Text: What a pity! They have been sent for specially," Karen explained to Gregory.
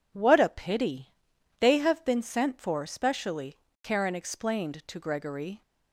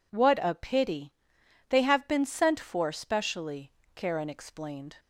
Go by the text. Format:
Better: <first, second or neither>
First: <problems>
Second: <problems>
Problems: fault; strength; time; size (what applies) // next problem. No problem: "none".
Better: first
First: none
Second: stops before "to Gregory"; at 4.9 s